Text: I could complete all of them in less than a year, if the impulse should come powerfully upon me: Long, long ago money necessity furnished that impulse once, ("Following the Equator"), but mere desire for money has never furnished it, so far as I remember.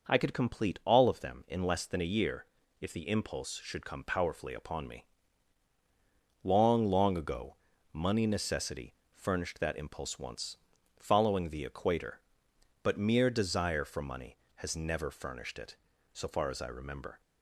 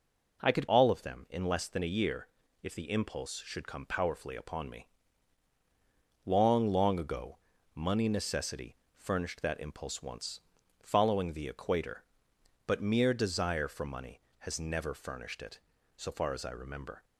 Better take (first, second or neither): first